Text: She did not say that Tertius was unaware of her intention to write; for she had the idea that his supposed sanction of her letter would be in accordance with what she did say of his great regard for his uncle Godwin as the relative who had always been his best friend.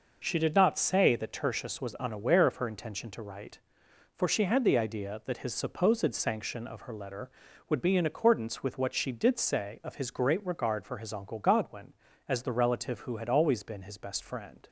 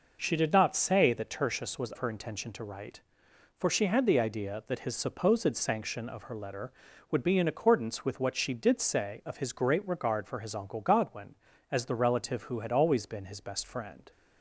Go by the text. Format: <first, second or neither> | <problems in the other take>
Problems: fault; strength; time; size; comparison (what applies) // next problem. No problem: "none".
first | skips "unaware of"; at 1.9 s